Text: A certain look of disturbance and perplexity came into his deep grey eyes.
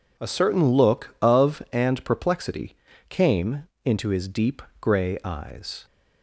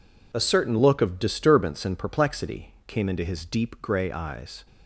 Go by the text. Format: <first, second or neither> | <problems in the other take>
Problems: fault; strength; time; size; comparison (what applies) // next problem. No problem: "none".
second | skips "disturbance"; at 1.6 s // pauses between "perplexity" and "came"; slight; at 2.7 s; 0.32 s long // pauses between "came" and "into"; slight; at 3.6 s; 0.18 s long // pauses between "deep" and "grey"; slight; at 4.6 s; 0.18 s long